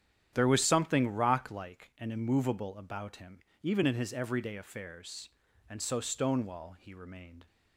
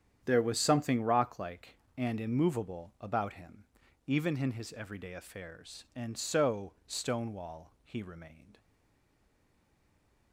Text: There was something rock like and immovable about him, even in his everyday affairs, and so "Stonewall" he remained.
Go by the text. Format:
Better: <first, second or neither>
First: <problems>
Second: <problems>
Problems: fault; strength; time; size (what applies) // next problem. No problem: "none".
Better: first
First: starts louder than the rest; strong; until 1.3 s; 10 dB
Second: starts louder than the rest; strong; until 1.2 s; 9 dB // stays silent after the last word; noticeable; from 8.5 s on; 1.8 s long